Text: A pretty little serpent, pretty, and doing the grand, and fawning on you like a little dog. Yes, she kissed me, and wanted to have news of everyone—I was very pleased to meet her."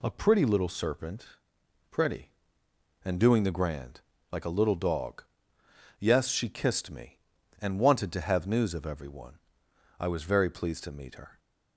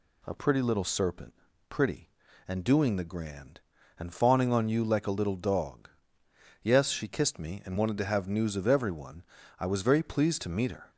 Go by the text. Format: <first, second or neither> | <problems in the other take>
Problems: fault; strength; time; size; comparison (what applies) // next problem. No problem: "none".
second | skips "and fawning on you"; at 4.1 s